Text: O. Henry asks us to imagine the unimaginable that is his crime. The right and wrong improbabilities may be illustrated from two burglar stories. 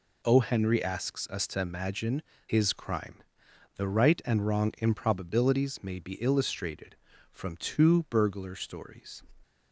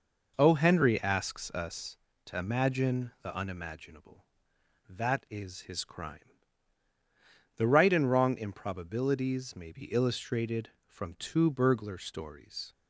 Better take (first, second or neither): second